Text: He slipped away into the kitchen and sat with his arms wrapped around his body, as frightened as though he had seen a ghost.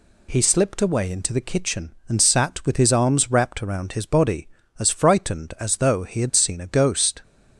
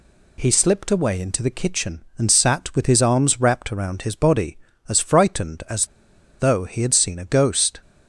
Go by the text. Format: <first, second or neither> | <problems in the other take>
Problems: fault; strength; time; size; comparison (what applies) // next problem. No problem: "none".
first | pauses between "as" and "though"; noticeable; at 5.8 s; 0.52 s long